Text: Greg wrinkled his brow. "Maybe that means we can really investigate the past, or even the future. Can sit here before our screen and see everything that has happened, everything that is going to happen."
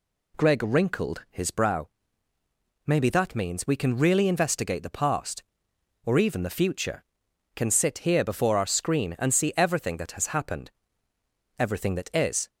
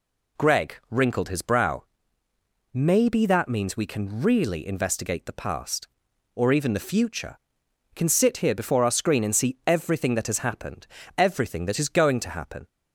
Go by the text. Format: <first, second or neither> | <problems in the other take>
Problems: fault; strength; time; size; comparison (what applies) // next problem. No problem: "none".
second | stops before "going to happen"; at 12.4 s